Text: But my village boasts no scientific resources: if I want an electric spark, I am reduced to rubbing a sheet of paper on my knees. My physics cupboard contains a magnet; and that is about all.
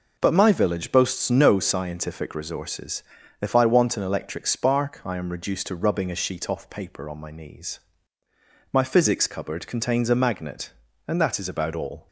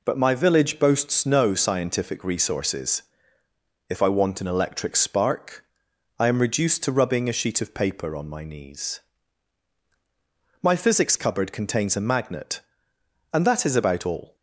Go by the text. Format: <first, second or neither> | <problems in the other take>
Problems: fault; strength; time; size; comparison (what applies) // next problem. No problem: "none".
second | says "off" for "of"; at 6.4 s